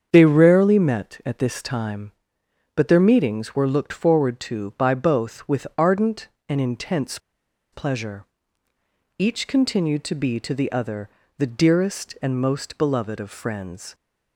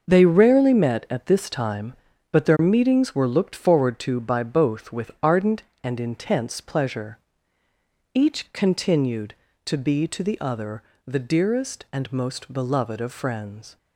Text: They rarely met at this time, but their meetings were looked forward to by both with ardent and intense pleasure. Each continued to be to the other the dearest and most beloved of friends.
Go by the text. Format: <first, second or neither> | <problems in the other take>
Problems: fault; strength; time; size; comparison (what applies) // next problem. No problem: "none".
second | starts louder than the rest; strong; until 1.1 s; 7.5 dB; also in the second // pauses between "intense" and "pleasure"; noticeable; at 7.1 s; 0.53 s long // pauses between "other" and "the"; slight; at 11.0 s; 0.30 s long; slight in the second